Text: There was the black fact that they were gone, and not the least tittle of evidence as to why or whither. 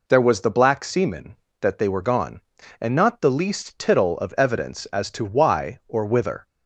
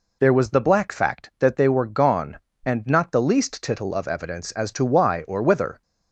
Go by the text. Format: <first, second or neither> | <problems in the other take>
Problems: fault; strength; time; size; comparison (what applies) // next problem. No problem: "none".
second | says "semen" for "fact"; at 0.8 s